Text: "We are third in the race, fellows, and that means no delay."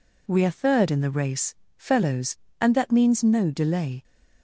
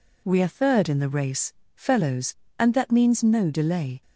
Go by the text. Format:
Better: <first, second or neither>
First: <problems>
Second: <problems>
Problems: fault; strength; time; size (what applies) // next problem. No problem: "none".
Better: neither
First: none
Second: none